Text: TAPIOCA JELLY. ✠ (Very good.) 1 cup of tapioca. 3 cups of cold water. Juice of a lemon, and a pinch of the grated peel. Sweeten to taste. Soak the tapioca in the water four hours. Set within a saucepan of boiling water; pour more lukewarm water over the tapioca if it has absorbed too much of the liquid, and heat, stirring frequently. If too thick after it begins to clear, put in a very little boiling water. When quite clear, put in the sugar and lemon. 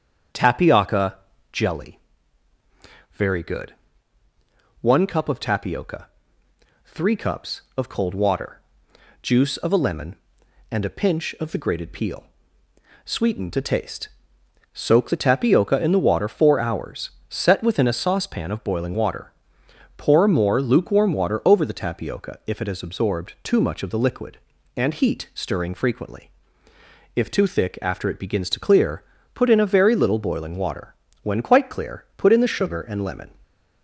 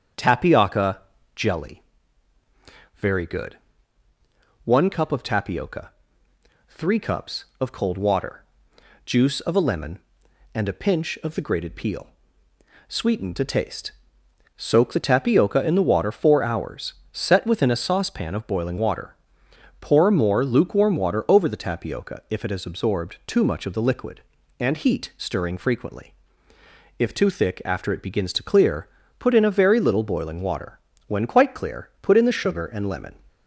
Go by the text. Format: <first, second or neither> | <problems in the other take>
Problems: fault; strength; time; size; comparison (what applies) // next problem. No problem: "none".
neither | starts louder than the rest; strong; the same in both // pauses between "TAPIOCA" and "JELLY"; slight; the same in both